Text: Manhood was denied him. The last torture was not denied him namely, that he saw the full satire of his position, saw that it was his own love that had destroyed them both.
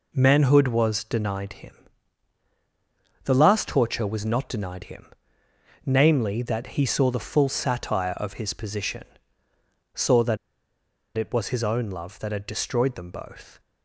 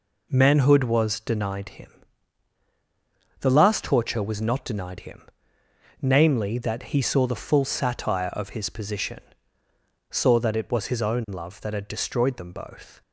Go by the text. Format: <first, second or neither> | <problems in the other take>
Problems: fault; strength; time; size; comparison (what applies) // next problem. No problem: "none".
second | pauses between "him" and "namely"; noticeable; at 5.0 s; 0.80 s long; noticeable in the second // pauses between "that" and "it"; noticeable; at 10.3 s; 0.78 s long